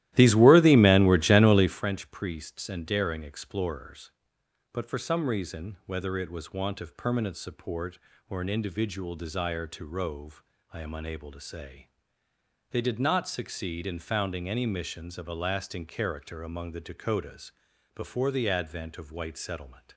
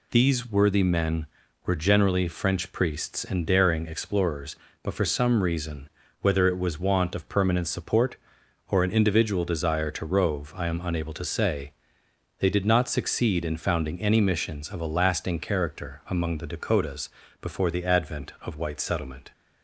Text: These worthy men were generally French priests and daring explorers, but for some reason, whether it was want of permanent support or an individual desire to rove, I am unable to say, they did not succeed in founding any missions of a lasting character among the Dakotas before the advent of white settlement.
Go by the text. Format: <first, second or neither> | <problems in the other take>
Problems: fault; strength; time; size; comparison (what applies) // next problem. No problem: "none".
second | starts louder than the rest; strong; until 1.8 s; 15 dB // pauses between "Dakotas" and "before"; at 17.5 s; 0.44 s long; slight in the second